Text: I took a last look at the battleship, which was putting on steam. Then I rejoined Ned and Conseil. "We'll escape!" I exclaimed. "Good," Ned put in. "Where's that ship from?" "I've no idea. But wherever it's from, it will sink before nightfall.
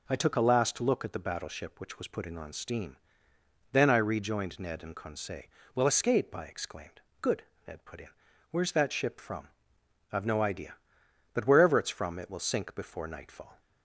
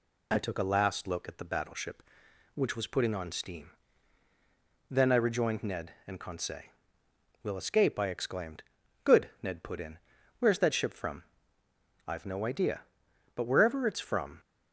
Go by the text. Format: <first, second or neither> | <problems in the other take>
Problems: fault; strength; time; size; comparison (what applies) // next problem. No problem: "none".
first | stops before "it will sink before nightfall"; at 14.3 s